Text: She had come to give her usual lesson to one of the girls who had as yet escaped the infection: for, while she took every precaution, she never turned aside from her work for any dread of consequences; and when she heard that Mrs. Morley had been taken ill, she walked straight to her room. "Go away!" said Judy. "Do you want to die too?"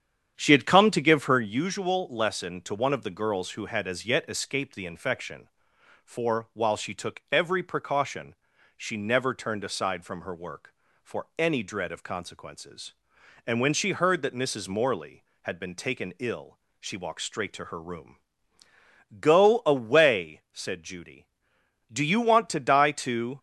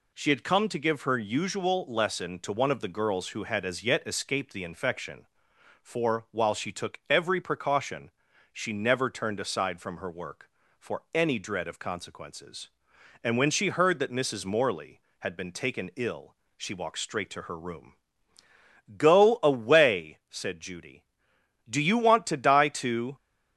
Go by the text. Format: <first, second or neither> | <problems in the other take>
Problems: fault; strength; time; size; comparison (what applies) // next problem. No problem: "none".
second | starts louder than the rest; strong; until 1.6 s; 8.5 dB